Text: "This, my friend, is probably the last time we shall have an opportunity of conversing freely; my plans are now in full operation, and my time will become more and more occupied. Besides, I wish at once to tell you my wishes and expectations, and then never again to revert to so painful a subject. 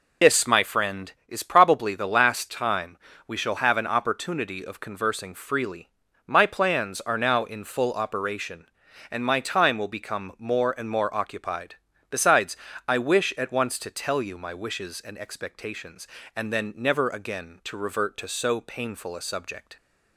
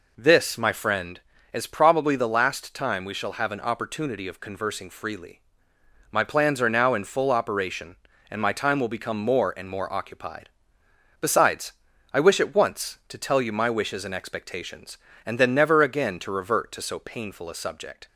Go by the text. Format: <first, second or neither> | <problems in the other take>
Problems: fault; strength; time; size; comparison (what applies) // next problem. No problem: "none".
second | loses the start of "This"; at 0.2 s; 50 ms // pauses between "time" and "we"; slight; at 2.9 s; 0.28 s long